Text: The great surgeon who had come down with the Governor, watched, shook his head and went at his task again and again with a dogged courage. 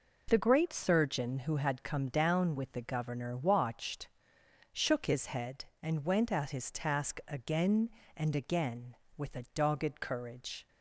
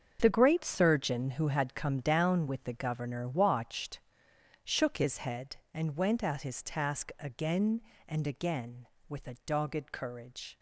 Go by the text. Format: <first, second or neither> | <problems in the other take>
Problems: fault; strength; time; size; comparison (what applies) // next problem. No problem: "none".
first | gets quieter; strong; throughout; 11.5 dB